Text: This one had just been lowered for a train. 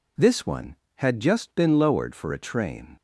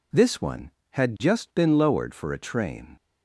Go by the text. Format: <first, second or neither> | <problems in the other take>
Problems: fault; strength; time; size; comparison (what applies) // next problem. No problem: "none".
neither | none